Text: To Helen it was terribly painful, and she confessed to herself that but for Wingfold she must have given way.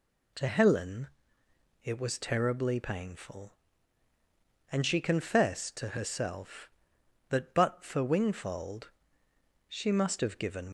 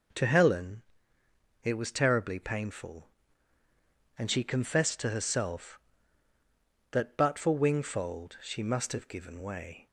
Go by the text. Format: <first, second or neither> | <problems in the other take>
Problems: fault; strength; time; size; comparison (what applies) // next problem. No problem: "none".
second | pauses between "Helen" and "it"; noticeable; at 1.0 s; 0.76 s long; noticeable in the second // pauses between "Wingfold" and "she"; noticeable; at 8.9 s; 0.78 s long // stops before "way"; at 10.6 s